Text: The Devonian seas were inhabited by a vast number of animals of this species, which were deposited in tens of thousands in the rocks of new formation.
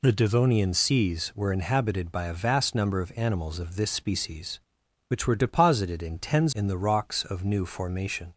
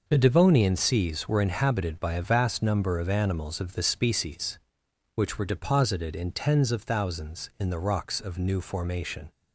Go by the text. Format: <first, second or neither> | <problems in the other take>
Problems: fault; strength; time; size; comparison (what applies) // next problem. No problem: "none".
second | skips "of thousands"; at 6.5 s